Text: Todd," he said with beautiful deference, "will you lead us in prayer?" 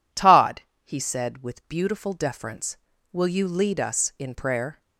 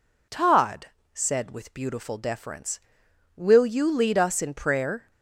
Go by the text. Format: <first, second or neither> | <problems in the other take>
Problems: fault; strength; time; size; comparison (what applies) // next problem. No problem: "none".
first | skips "he"; at 1.0 s